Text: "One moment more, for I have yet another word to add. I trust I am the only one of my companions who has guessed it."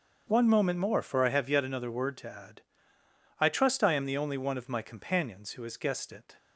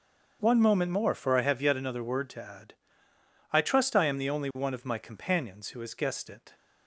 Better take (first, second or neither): neither